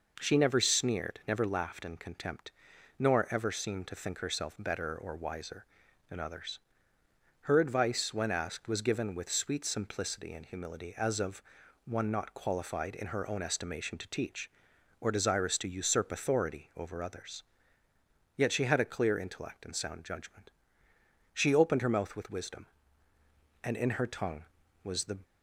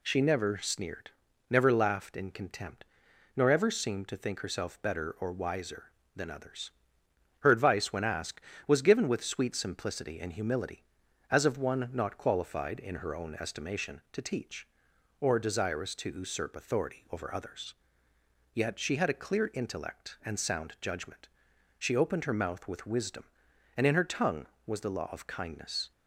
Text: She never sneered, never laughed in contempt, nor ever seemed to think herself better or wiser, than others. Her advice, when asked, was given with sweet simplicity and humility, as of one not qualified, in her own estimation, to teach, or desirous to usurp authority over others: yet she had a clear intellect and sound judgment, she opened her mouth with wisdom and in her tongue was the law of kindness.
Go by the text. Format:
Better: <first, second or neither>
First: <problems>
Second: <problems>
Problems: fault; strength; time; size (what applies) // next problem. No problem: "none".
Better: second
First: pauses between "of" and "one"; at 11.4 s; 0.44 s long // stops before "law of kindness"; at 25.2 s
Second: none